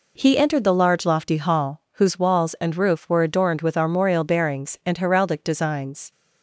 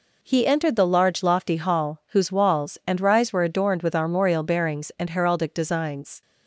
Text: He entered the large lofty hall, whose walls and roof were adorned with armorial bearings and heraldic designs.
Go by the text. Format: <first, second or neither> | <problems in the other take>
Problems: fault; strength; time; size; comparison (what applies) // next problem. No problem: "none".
first | says "rise" for "roof"; at 3.0 s